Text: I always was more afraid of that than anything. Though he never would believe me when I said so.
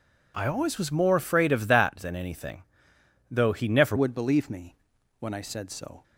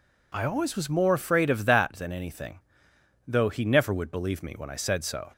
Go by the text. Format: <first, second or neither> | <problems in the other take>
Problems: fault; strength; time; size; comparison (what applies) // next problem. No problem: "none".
second | changes voice at "would"; from 3.9 s on; 2.1 s long // pauses between "me" and "when"; at 4.7 s; 0.44 s long